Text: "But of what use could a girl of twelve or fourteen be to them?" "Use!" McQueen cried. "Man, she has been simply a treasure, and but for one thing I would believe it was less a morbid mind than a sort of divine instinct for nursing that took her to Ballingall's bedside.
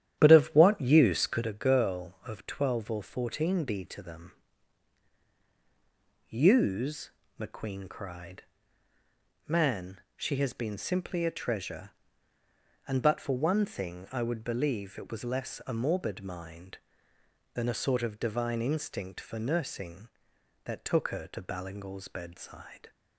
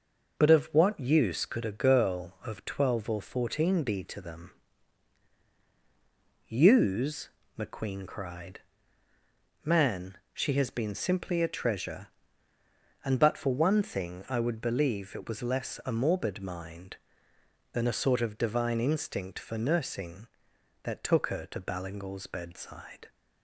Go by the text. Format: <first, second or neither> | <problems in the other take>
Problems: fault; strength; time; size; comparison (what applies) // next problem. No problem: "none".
second | starts louder than the rest; strong; until 1.5 s; 11 dB